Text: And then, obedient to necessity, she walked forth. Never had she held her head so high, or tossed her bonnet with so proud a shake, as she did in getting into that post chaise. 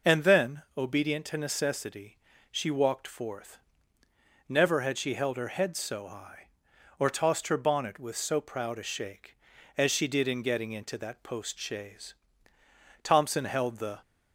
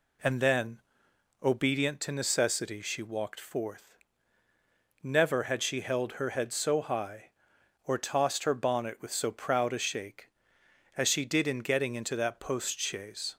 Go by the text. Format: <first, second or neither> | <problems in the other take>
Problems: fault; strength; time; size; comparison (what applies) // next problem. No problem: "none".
second | goes on to say "Thompson held the"; noticeable; from 13.0 s on; 0.96 s long